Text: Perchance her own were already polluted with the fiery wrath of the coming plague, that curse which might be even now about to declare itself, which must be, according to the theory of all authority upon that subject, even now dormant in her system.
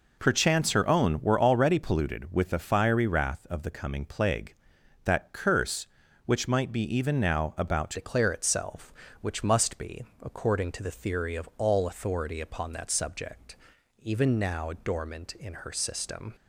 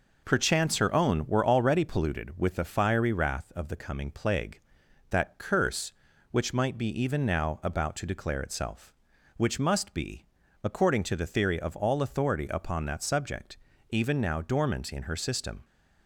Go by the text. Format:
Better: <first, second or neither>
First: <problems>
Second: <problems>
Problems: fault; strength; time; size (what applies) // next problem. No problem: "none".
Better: second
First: changes voice at "declare"; from 7.9 s on; 8.4 s long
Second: none